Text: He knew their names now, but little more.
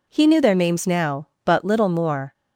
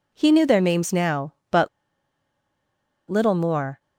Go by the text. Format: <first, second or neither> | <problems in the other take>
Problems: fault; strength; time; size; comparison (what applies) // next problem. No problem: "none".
first | pauses between "but" and "little"; strong; at 1.6 s; 1.4 s long